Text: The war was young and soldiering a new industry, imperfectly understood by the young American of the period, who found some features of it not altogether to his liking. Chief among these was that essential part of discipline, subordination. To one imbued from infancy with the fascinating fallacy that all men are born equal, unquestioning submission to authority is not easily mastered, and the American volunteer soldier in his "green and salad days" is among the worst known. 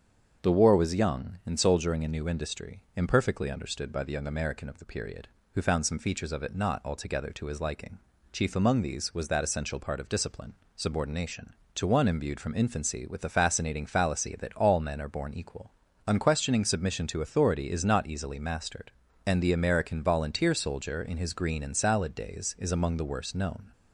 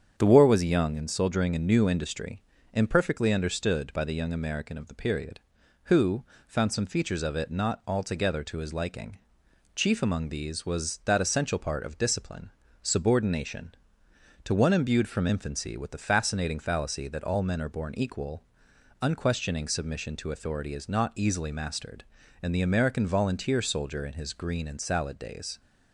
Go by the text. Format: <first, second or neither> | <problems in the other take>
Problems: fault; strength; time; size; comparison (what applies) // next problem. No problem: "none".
first | starts louder than the rest; strong; until 1.1 s; 8 dB; also in the first // pauses between "who" and "found"; slight; at 6.2 s; 0.22 s long // stops before "is among the worst known"; at 25.5 s